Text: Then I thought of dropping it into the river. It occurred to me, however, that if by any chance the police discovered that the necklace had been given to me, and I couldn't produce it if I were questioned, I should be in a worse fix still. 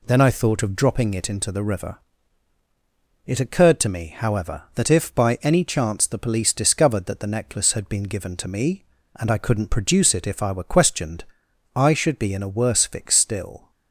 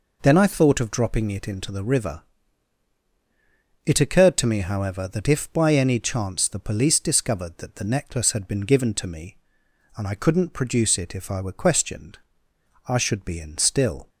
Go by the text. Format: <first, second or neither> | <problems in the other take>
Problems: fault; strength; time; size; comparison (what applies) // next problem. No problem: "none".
first | skips "a worse fix"; at 13.5 s